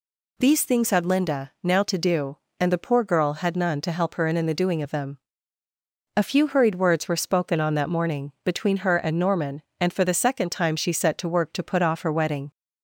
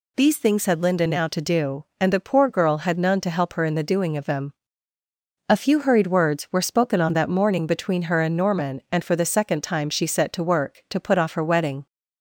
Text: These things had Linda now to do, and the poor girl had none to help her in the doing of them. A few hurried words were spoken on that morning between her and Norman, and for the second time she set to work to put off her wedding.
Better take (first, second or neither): second